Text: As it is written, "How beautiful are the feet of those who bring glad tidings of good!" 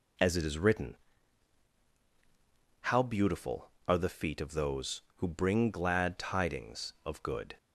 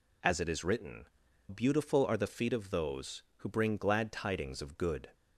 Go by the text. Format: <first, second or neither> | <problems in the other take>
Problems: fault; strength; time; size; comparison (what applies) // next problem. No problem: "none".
first | skips "How"; at 1.2 s